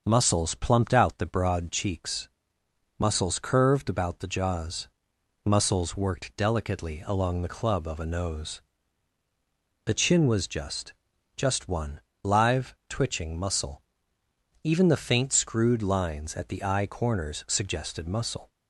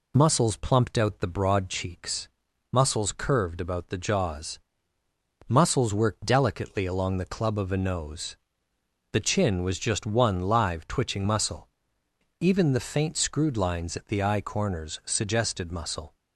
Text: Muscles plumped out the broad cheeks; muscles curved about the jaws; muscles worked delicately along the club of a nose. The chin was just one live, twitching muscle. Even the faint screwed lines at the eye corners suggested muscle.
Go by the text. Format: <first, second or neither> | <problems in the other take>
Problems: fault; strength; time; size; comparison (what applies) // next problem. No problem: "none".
second | starts louder than the rest; until 1.0 s; 6.5 dB // says "just" twice; at 11.3 s // pauses between "one" and "live"; slight; at 12.0 s; 0.20 s long